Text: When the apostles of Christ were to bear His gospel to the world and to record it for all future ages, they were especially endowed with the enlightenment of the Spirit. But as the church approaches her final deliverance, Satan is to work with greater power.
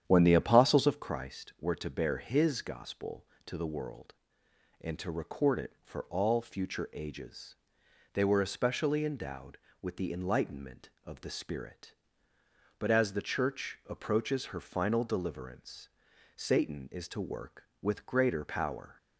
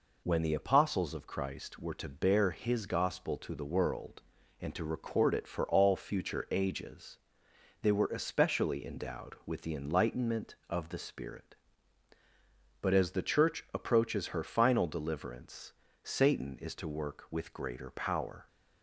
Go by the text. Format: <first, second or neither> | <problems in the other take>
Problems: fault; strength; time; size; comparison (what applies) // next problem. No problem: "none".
second | starts louder than the rest; strong; until 1.0 s; 9.5 dB